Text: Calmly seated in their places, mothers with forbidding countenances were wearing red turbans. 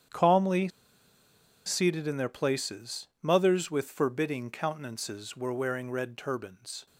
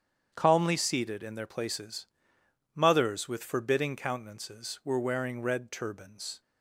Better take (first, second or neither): second